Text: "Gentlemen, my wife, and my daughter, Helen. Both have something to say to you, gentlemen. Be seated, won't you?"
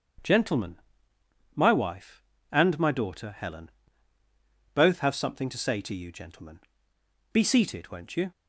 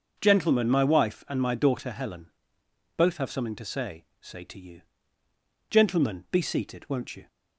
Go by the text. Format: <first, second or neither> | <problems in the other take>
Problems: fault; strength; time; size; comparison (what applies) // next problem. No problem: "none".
first | starts louder than the rest; until 1.2 s; 6 dB; strong in the first // says "say" twice; at 4.1 s